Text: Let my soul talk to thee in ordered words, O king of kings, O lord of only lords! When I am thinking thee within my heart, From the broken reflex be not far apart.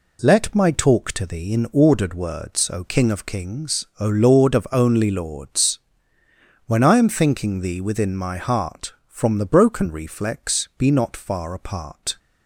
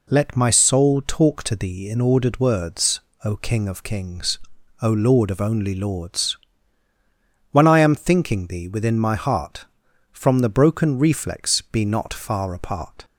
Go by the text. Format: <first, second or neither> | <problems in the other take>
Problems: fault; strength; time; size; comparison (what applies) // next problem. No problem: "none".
second | skips "soul"; at 0.7 s